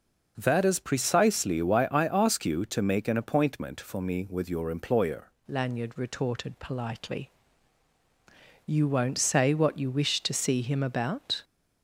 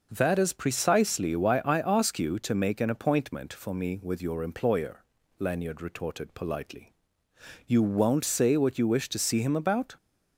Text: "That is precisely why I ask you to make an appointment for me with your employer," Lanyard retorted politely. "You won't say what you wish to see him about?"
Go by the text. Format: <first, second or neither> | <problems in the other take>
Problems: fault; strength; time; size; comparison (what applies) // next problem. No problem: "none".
second | changes voice at "Lanyard"; from 5.4 s on; 6.0 s long